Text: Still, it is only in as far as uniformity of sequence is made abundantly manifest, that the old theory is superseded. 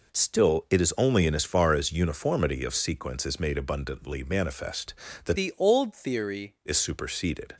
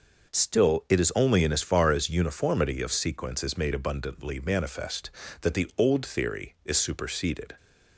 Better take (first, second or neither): second